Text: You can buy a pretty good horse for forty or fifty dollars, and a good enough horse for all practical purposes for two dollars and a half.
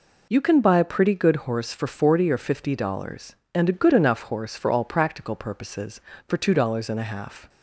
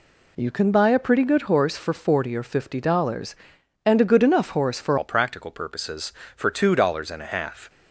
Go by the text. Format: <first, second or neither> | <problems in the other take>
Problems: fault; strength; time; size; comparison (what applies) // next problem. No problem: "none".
first | changes voice at "all"; from 4.9 s on; 2.7 s long